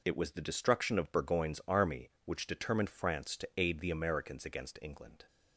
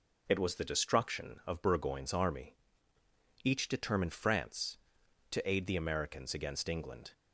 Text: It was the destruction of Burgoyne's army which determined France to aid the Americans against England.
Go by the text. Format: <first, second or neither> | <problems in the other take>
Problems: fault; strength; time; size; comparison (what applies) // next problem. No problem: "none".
first | says "each" for "which"; at 3.4 s